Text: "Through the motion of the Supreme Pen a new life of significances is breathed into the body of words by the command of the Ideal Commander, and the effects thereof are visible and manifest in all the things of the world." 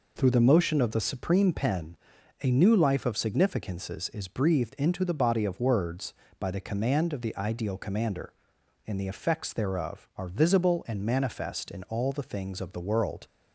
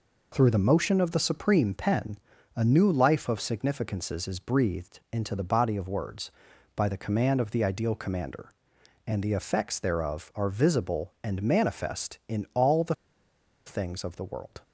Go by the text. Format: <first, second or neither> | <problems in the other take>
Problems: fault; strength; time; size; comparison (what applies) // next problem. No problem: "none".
first | pauses between "Pen" and "a"; at 2.1 s; 0.38 s long; noticeable in the first // pauses between "the" and "things"; noticeable; at 12.9 s; 0.71 s long